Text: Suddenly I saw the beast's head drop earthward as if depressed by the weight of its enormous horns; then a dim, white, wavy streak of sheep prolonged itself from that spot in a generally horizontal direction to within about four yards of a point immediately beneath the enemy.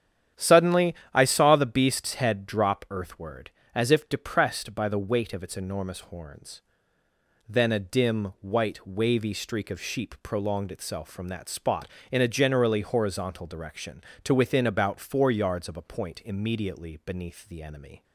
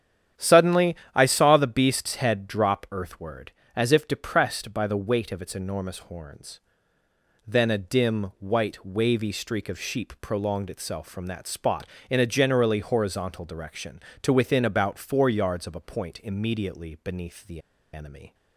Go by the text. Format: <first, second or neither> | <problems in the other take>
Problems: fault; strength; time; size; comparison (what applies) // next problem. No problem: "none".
first | starts louder than the rest; strong; until 1.5 s; 9.5 dB; strong in the first // pauses between "Suddenly" and "I"; slight; at 0.9 s; 0.18 s long; slight in the first // pauses between "the" and "enemy"; slight; at 17.6 s; 0.32 s long